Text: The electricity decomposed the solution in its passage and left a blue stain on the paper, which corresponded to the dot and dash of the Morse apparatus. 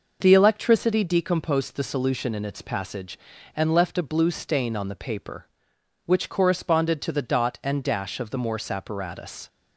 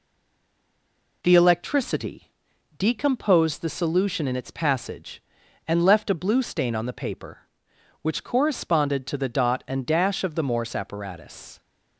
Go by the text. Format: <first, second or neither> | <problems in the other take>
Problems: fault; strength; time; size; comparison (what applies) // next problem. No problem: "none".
first | stays silent before the first word; noticeable; until 1.2 s; 1.2 s long // pauses between "electricity" and "decomposed"; noticeable; at 2.3 s; 0.46 s long